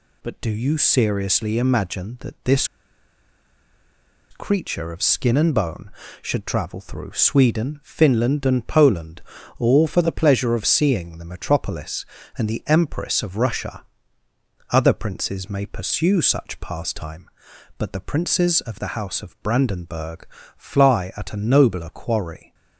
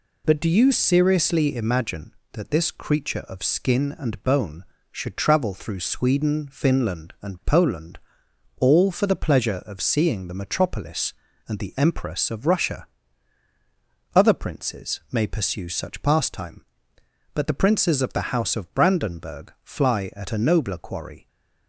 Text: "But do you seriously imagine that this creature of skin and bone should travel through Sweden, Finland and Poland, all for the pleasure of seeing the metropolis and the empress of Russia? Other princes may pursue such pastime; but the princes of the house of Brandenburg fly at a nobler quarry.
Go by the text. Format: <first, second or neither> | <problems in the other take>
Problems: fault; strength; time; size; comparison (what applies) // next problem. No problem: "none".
second | pauses between "this" and "creature"; strong; at 2.6 s; 1.6 s long // pauses between "Brandenburg" and "fly"; slight; at 20.2 s; 0.30 s long